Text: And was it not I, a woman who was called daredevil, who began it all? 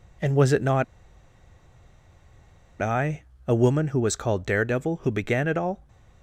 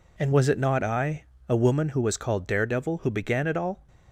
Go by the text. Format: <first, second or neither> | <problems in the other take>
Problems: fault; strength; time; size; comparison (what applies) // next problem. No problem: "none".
second | pauses between "not" and "I"; strong; at 0.8 s; 1.9 s long